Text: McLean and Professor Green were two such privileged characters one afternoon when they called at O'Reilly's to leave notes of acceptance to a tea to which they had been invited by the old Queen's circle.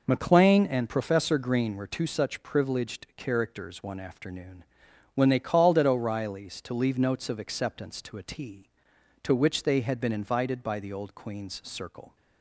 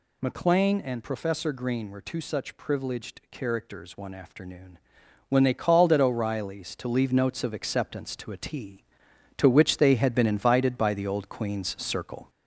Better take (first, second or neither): first